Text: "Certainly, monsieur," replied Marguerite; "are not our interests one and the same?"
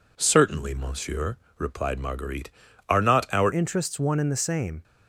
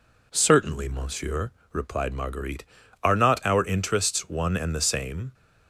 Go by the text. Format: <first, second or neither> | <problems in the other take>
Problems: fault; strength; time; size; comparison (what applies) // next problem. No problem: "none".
second | changes voice at "interests"; from 3.5 s on; 1.3 s long